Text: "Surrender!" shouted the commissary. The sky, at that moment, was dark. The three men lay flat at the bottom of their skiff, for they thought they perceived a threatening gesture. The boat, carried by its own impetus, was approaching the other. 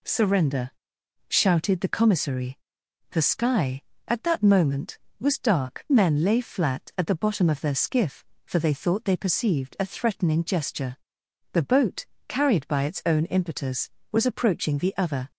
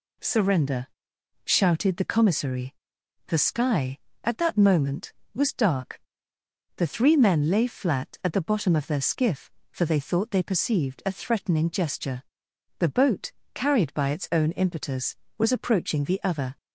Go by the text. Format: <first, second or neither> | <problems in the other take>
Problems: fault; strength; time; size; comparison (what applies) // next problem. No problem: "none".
second | skips "The three"; at 5.8 s